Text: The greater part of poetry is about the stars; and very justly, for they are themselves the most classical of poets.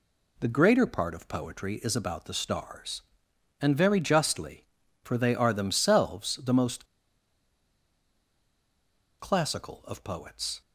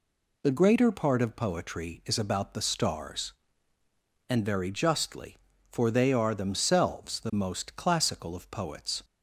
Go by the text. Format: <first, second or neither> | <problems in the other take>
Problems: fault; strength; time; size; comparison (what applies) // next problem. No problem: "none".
second | pauses between "most" and "classical"; strong; at 6.8 s; 2.3 s long